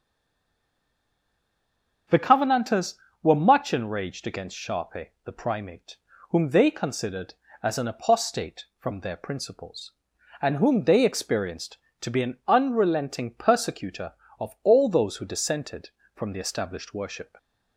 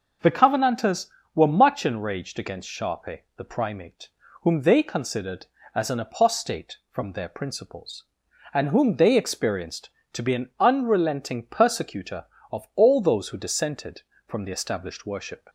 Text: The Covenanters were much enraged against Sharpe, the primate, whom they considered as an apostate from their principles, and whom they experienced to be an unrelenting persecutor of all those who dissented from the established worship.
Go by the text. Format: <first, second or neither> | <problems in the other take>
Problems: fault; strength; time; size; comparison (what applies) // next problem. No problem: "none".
second | stays silent before the first word; noticeable; until 2.0 s; 2.0 s long // starts louder than the rest; noticeable; until 3.3 s; 6 dB; noticeable in the second